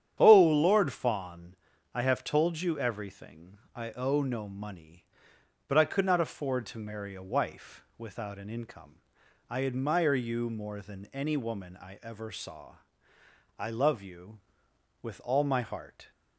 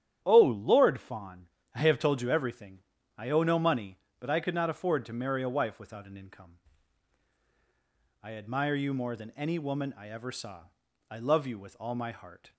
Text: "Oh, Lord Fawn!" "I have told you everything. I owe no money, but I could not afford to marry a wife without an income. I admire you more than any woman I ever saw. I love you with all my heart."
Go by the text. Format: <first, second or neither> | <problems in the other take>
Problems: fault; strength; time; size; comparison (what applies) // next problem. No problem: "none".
neither | starts louder than the rest; strong; the same in both